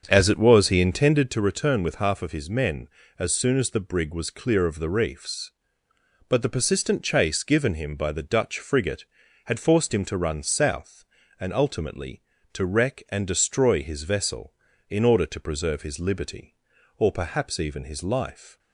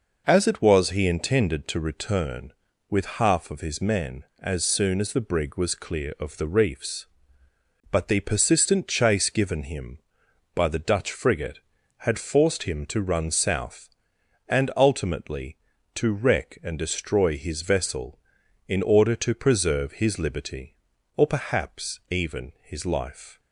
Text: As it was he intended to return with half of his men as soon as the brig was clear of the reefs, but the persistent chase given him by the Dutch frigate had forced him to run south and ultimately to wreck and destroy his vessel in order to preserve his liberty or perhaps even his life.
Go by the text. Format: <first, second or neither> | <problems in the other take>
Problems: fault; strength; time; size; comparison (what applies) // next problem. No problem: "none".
second | starts louder than the rest; until 1.3 s; 7 dB